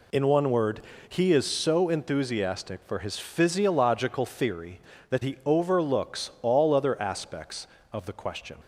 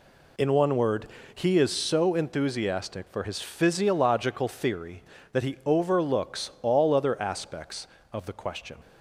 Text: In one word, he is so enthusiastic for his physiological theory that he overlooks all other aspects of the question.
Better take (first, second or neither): neither